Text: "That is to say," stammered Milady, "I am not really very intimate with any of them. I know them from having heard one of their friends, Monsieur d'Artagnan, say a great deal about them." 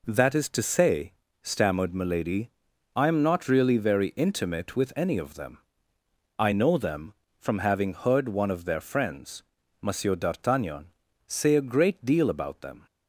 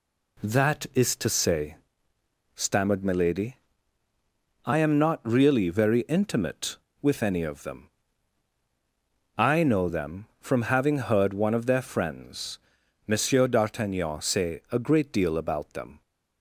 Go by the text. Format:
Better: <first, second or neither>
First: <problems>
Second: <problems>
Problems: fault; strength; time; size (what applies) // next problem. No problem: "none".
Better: neither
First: none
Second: none